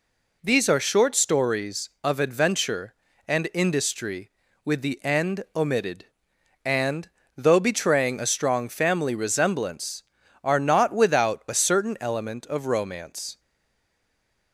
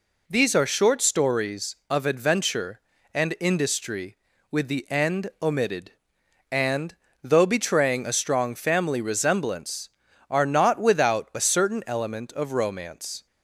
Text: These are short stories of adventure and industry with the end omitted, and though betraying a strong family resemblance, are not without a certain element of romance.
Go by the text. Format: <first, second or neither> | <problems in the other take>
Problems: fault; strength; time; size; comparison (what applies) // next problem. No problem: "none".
second | pauses between "and" and "though"; slight; at 7.0 s; 0.26 s long; slight in the second // stays silent after the last word; noticeable; from 13.3 s on; 1.2 s long